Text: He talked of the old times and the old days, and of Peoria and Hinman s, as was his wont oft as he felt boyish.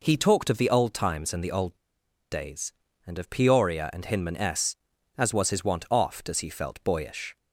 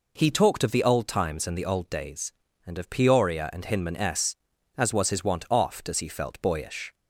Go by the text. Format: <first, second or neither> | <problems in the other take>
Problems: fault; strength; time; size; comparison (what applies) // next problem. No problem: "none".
second | pauses between "old" and "days"; noticeable; at 1.7 s; 0.55 s long